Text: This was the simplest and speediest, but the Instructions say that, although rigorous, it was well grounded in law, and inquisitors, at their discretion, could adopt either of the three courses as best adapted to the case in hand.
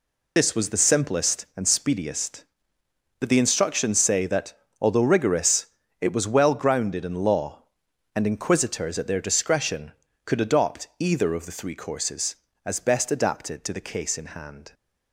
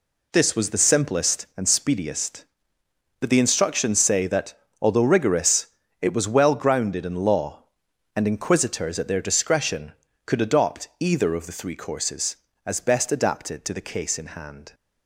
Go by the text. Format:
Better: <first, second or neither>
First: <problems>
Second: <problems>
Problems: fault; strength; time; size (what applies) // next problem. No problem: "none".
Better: second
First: loses the start of "This"; at 0.3 s; 45 ms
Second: none